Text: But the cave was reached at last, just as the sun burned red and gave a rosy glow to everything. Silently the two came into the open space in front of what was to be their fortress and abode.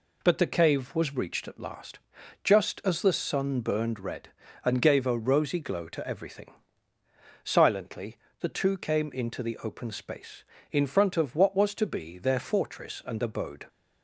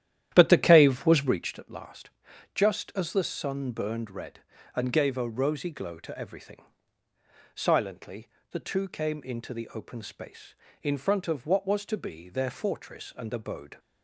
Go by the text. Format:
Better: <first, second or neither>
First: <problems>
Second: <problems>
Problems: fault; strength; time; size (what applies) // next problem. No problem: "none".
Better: first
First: pauses between "Silently" and "the"; slight; at 8.1 s; 0.24 s long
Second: starts louder than the rest; strong; until 1.5 s; 11.5 dB // pauses between "Silently" and "the"; slight; at 8.2 s; 0.24 s long